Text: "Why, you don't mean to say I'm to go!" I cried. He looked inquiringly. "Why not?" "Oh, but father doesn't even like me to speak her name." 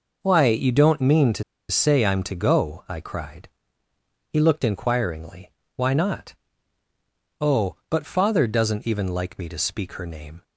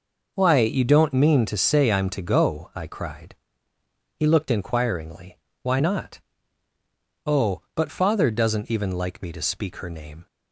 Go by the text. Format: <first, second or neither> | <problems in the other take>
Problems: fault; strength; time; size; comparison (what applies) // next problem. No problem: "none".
second | pauses between "to" and "say"; slight; at 1.4 s; 0.27 s long